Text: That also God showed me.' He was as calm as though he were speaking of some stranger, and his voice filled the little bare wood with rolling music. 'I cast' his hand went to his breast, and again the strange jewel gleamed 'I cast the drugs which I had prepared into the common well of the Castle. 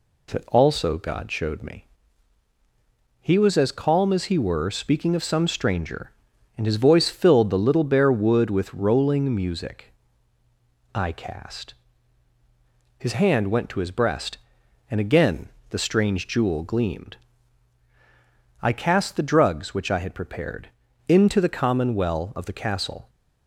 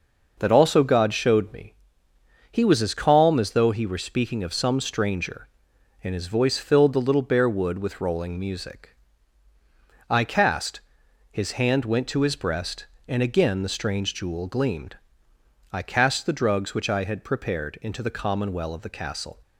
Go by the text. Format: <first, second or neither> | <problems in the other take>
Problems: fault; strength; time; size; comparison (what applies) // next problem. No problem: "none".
second | skips "though"; at 4.2 s // pauses between "cast" and "his"; strong; at 11.7 s; 1.2 s long; noticeable in the second // pauses between "again" and "the"; slight; at 15.4 s; 0.22 s long // pauses between "gleamed" and "I"; strong; at 17.1 s; 1.4 s long; noticeable in the second // pauses between "prepared" and "into"; at 20.6 s; 0.38 s long